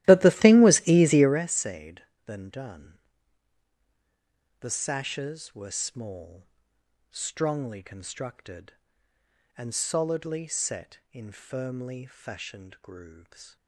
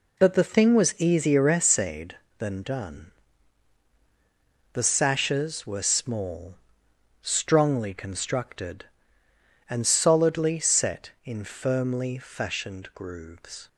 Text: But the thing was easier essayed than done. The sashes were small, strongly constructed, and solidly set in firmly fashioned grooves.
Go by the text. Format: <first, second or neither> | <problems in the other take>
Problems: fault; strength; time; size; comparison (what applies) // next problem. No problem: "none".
second | starts louder than the rest; strong; until 1.4 s; 14.5 dB